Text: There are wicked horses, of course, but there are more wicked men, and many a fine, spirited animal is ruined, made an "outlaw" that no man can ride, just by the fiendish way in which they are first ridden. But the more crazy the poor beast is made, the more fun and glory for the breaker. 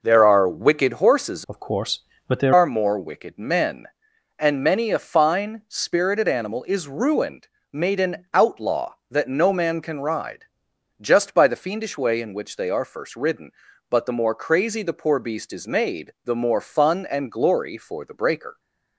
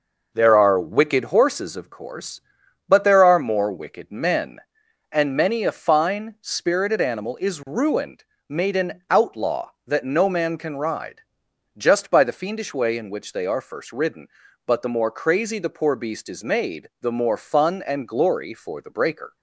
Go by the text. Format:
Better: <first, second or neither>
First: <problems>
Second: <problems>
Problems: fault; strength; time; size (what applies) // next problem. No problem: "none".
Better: second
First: changes voice from "of" to "there"; from 1.4 to 2.5 s; 1.1 s long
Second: none